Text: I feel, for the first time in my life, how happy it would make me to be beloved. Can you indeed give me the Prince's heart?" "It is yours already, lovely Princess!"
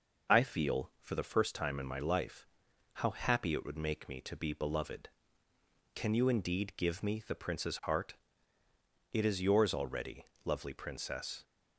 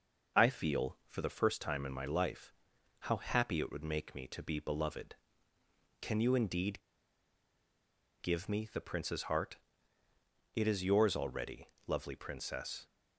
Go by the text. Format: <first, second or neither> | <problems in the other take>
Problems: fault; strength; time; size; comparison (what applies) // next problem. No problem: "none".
first | pauses between "indeed" and "give"; strong; at 6.8 s; 1.4 s long